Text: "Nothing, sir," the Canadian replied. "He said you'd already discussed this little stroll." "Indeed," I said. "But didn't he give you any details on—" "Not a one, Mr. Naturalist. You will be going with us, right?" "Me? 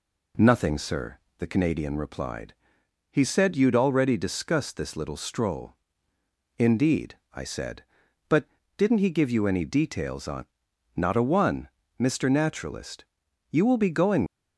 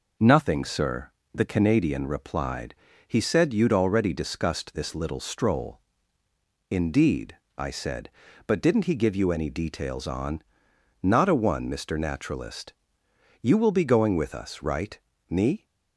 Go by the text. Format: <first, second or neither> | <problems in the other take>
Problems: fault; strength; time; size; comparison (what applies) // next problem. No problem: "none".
second | pauses between "But" and "didn't"; slight; at 8.4 s; 0.30 s long // stops before "with us right Me"; at 14.2 s